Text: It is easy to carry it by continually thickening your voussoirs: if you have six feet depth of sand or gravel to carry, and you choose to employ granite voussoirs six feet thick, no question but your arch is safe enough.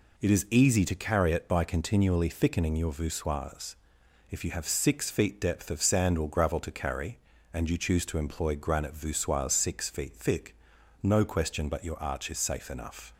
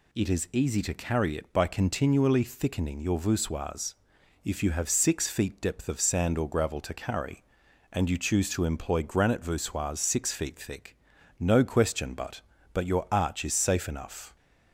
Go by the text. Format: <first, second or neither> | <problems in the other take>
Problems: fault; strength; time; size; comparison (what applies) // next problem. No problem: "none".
first | says "but" twice; at 12.7 s